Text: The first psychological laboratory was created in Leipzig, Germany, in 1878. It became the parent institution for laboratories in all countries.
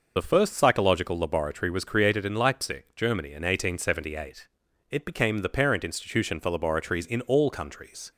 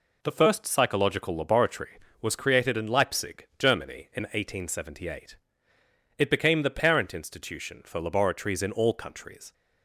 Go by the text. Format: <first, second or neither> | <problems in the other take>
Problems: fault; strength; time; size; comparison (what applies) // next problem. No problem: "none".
second | loses the start of "The"; at 0.1 s; 35 ms